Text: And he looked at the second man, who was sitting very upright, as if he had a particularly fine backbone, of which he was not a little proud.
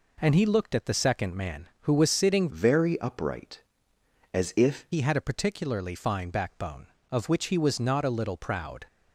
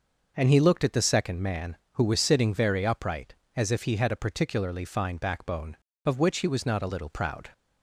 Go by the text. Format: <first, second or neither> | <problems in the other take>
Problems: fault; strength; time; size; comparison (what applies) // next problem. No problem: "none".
second | changes voice from "very" to "if"; from 2.4 to 4.8 s; 2.4 s long